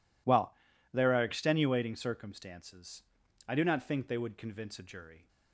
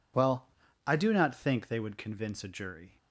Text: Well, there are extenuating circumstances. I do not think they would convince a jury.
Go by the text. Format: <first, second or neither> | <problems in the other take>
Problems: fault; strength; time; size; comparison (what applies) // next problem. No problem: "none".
first | skips "there are extenuating circumstances"; at 0.6 s